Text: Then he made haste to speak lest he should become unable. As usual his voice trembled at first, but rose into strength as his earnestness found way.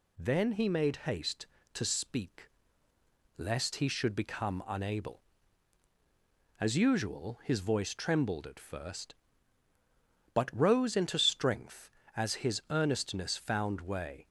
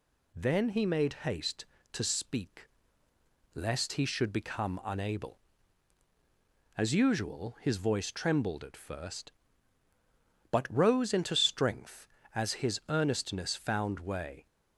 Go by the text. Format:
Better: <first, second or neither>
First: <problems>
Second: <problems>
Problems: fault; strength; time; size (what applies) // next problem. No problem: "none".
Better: neither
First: pauses between "speak" and "lest"; noticeable; at 2.4 s; 0.90 s long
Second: pauses between "speak" and "lest"; noticeable; at 2.6 s; 0.88 s long